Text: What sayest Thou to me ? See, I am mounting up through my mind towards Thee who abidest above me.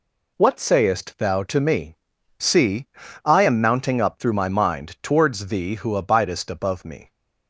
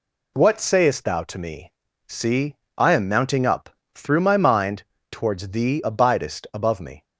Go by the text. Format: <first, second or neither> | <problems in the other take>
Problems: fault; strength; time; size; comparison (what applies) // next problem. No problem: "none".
first | pauses between "up" and "through"; slight; at 3.6 s; 0.24 s long // pauses between "mind" and "towards"; slight; at 4.8 s; 0.30 s long // skips "who"; at 5.8 s